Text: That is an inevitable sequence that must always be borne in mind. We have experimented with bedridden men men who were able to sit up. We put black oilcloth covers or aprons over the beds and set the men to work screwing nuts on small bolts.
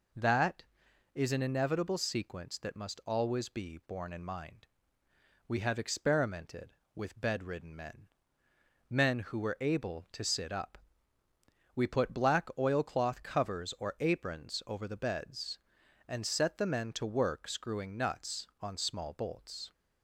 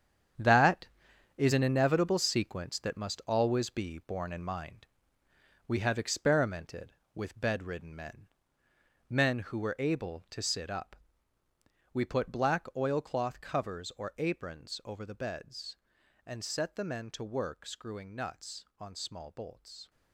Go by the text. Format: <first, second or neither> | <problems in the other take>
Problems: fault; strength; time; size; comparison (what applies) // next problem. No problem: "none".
first | gets quieter; strong; throughout; 11 dB // pauses between "men" and "men"; noticeable; at 8.2 s; 0.82 s long; noticeable in the first